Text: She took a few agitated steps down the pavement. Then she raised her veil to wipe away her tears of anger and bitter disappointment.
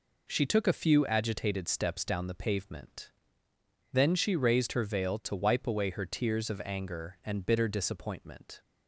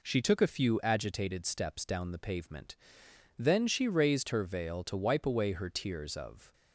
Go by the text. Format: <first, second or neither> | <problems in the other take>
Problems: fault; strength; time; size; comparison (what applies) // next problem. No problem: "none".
first | stops before "anger and bitter disappointment"; at 6.5 s